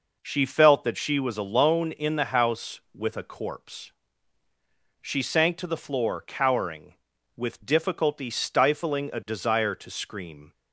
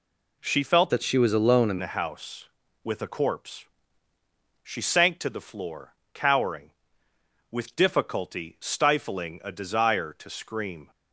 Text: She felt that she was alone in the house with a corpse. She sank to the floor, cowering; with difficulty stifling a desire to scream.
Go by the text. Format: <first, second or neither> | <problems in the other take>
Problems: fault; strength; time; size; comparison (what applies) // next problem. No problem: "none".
first | changes voice from "that" to "in"; from 0.8 to 1.7 s; 0.9 s long